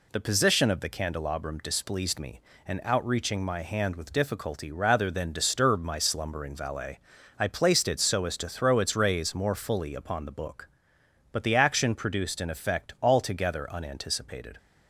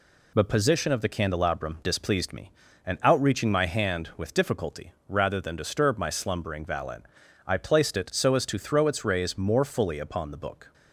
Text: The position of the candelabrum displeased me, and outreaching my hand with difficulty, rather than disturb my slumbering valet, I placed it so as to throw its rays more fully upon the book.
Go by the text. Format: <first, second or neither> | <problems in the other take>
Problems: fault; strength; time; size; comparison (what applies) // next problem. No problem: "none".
second | goes on to say "But the action produced an effect altogether unanticipated"; strong; from 11.3 s on; 3.2 s long